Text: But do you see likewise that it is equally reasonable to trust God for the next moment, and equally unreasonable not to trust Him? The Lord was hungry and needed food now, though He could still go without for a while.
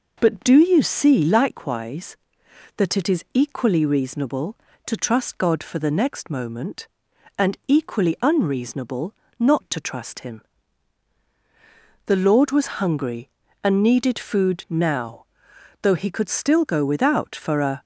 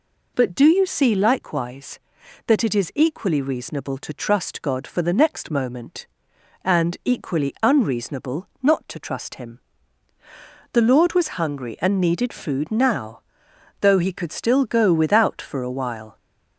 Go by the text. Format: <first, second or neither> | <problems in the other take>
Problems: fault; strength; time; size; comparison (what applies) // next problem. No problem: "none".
second | pauses between "unreasonable" and "not"; slight; at 9.1 s; 0.26 s long // stops before "while"; at 17.8 s